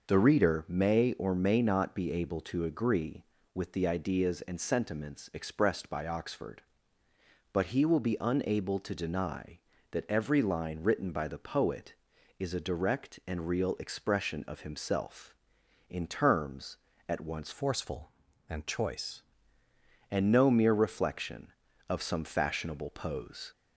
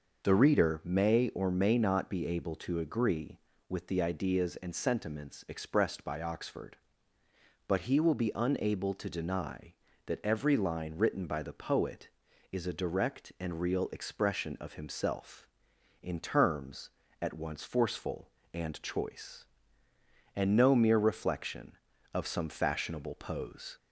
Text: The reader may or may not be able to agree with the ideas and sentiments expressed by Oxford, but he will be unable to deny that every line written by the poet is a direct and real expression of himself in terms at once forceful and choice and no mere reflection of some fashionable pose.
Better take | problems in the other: second | changes voice from "forceful" to "choice"; from 17.5 to 19.2 s; 1.7 s long

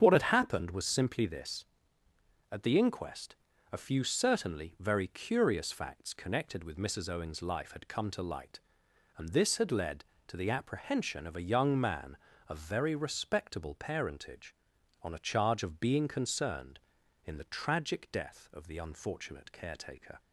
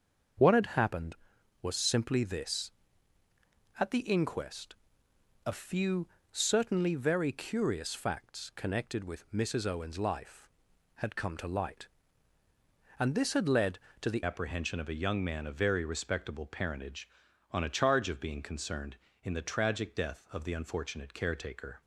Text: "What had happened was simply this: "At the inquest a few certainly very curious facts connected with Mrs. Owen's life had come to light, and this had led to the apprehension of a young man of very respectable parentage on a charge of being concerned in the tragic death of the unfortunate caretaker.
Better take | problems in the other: first | starts louder than the rest; until 1.8 s; 6.5 dB; strong in the first // pauses between "inquest" and "a"; noticeable; at 4.7 s; 0.68 s long; slight in the first // pauses between "few" and "certainly"; slight; at 6.0 s; 0.24 s long // changes voice at "apprehension"; from 14.2 s on; 7.6 s long

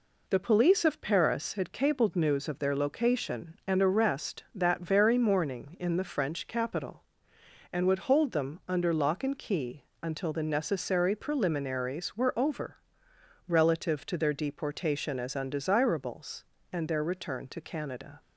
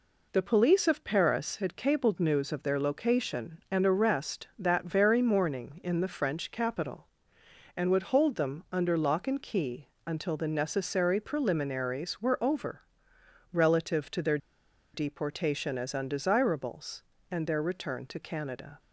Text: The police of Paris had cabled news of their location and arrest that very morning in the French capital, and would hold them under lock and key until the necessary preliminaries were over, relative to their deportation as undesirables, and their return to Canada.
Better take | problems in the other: first | pauses between "key" and "until"; slight; at 9.8 s; 0.18 s long; slight in the first // pauses between "their" and "deportation"; noticeable; at 14.3 s; 0.56 s long

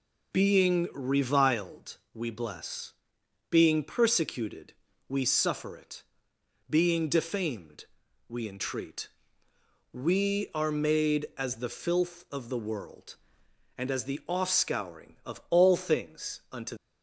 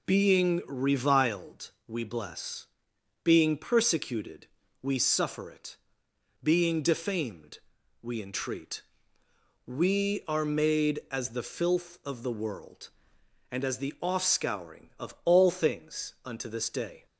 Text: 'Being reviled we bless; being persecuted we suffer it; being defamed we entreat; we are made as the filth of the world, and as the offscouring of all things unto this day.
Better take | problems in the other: second | pauses between "reviled" and "we"; slight; at 1.9 s; 0.16 s long; slight in the second // pauses between "persecuted" and "we"; at 4.7 s; 0.38 s long; also in the second // pauses between "defamed" and "we"; noticeable; at 7.8 s; 0.46 s long; noticeable in the second // stops before "this day"; at 16.7 s

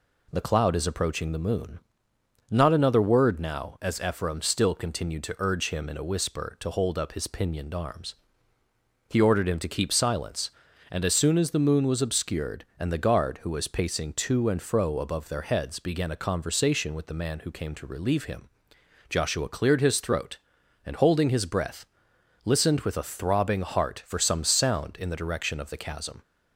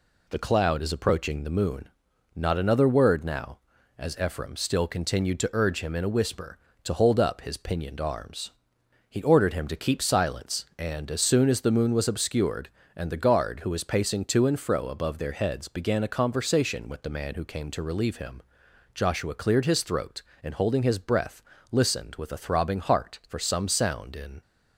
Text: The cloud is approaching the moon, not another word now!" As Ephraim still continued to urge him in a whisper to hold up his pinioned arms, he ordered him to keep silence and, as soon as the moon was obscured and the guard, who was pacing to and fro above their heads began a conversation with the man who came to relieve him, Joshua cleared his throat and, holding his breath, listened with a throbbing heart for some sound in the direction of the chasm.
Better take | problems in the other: first | stops before "the direction of the chasm"; at 24.4 s

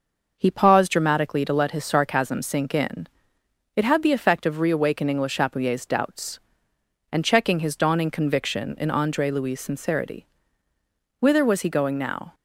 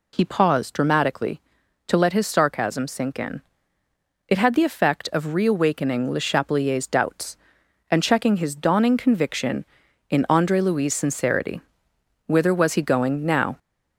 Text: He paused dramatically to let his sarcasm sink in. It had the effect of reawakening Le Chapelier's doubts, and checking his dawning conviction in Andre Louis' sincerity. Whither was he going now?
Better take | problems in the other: first | gets louder; slight; throughout; 3 dB

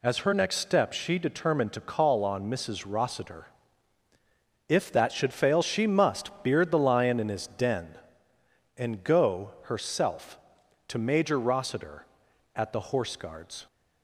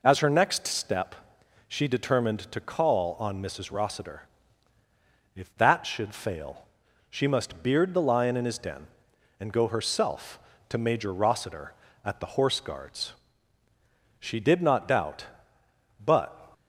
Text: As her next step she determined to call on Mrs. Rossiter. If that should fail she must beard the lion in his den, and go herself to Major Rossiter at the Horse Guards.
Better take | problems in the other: first | pauses between "step" and "she"; noticeable; at 1.1 s; 0.52 s long // pauses between "fail" and "she"; noticeable; at 6.6 s; 0.46 s long // goes on to say "She did not doubt but"; strong; from 14.1 s on; 2.2 s long

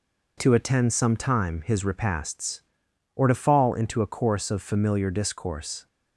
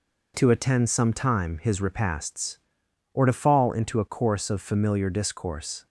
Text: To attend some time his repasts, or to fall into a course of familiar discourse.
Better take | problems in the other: neither | none

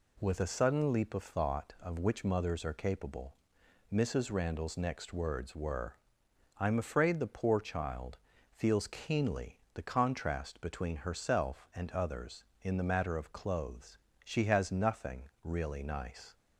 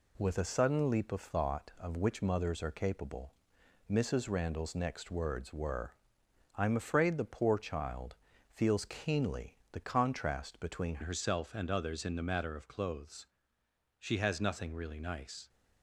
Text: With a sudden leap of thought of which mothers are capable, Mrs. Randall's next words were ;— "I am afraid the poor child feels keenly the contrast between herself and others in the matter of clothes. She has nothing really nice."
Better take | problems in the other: first | pauses between "child" and "feels"; slight; at 8.1 s; 0.36 s long; slight in the first // changes voice at "herself"; from 11.0 s on; 4.4 s long

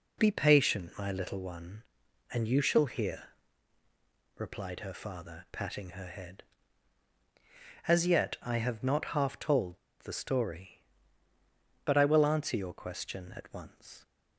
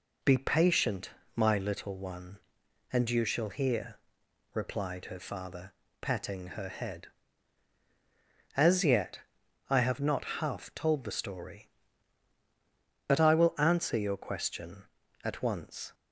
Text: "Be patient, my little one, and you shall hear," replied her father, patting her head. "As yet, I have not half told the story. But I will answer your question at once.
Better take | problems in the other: second | pauses between "told" and "the"; slight; at 9.7 s; 0.22 s long

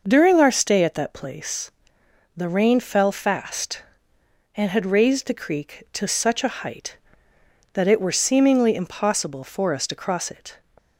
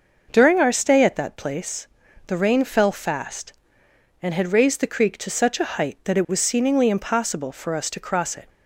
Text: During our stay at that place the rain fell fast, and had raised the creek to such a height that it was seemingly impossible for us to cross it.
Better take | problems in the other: second | pauses between "place" and "the"; noticeable; at 1.6 s; 0.64 s long; also in the second // says "were" for "was"; at 7.9 s

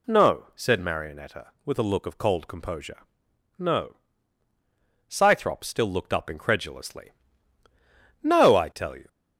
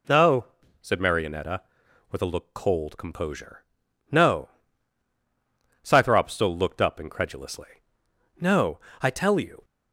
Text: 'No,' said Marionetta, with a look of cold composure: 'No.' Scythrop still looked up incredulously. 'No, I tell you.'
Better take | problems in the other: first | skips "of"; at 2.5 s

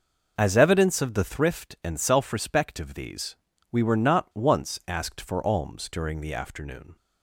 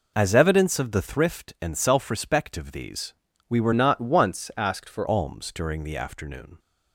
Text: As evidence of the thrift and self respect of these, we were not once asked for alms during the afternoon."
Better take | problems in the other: first | changes voice from "not" to "for"; from 3.7 to 5.0 s; 1.3 s long

